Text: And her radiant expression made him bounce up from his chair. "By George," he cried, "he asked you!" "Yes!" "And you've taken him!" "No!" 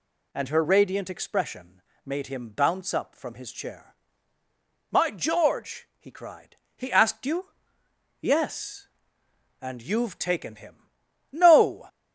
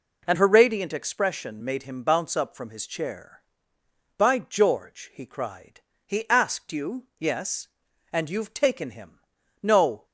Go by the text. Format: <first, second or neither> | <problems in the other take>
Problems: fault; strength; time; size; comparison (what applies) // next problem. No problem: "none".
second | pauses between "expression" and "made"; slight; at 1.8 s; 0.22 s long // says "My" for "By"; at 4.8 s